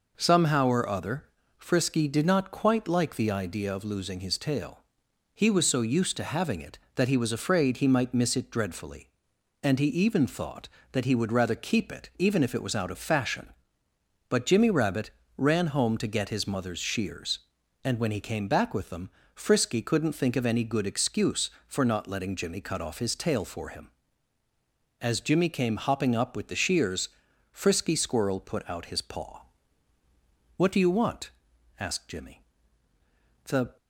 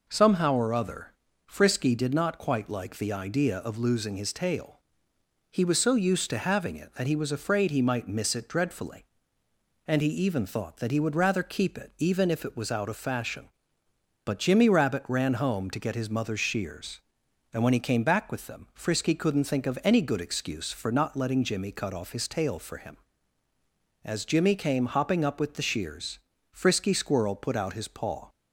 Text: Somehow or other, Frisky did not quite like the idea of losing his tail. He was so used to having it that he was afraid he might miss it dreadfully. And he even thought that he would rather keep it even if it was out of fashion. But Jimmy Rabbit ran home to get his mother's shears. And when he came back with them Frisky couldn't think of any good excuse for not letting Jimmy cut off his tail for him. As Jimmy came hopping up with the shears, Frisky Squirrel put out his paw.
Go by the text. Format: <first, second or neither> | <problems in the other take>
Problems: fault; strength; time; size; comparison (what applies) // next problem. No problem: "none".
second | pauses between "Rabbit" and "ran"; slight; at 15.0 s; 0.26 s long // pauses between "them" and "Frisky"; slight; at 19.0 s; 0.24 s long // goes on to say "What do you want asked Jimmy The"; strong; from 30.5 s on; 3.2 s long